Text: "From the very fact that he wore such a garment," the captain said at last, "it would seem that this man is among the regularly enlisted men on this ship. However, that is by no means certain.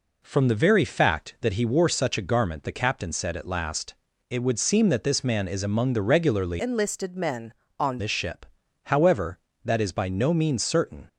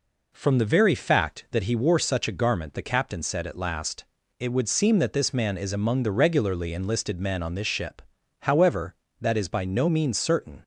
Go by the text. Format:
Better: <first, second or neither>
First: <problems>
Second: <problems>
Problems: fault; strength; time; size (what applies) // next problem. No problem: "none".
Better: second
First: changes voice from "enlisted" to "on"; from 6.5 to 7.9 s; 1.4 s long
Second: none